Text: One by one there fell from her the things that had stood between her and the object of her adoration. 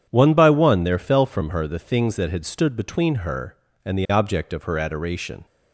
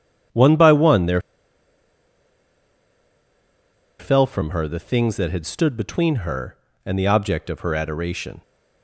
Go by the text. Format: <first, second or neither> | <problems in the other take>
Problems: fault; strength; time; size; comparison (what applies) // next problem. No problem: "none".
first | starts louder than the rest; strong; until 4.1 s; 8.5 dB; strong in the first // pauses between "there" and "fell"; strong; at 1.1 s; 2.7 s long